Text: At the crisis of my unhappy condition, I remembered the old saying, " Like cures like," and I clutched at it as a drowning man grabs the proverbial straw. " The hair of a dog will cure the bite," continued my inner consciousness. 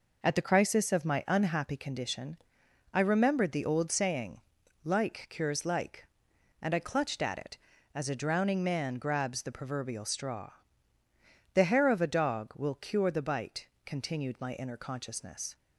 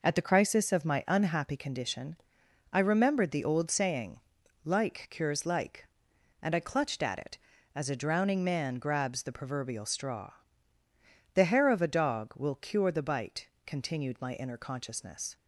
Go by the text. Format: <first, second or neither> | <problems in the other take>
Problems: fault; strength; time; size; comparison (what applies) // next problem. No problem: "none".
neither | none